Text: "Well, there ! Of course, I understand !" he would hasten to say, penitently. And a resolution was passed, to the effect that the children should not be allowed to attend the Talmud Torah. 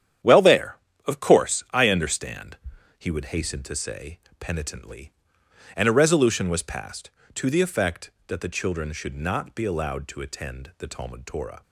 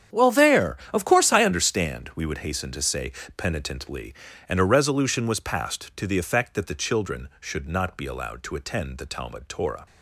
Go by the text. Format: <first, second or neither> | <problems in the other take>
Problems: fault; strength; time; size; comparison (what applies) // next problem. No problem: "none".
first | starts louder than the rest; strong; until 1.3 s; 9 dB; strong in the first // says "we" for "he"; at 2.1 s